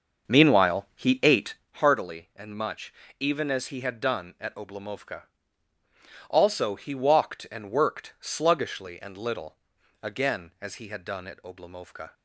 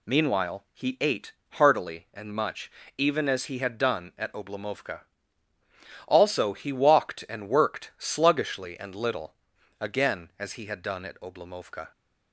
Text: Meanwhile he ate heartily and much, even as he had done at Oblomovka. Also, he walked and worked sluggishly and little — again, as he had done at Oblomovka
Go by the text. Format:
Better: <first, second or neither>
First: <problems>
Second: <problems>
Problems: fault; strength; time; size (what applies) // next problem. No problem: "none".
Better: second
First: starts louder than the rest; until 1.7 s; 6.5 dB // pauses between "ate" and "heartily"; slight; at 1.5 s; 0.22 s long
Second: pauses between "ate" and "heartily"; slight; at 1.3 s; 0.22 s long